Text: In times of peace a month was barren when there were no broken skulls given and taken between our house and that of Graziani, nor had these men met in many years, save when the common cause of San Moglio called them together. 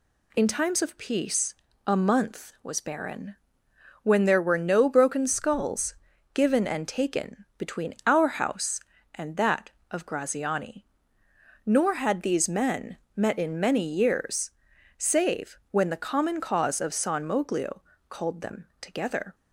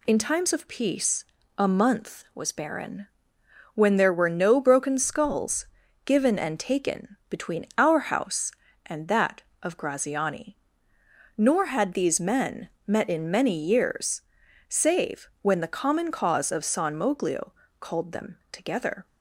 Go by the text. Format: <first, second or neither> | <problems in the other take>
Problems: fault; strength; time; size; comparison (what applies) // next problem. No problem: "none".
neither | pauses between "peace" and "a"; slight; the same in both // pauses between "barren" and "when"; noticeable; the same in both // pauses between "skulls" and "given"; the same in both // pauses between "men" and "met"; slight; the same in both // pauses between "Moglio" and "called"; slight; the same in both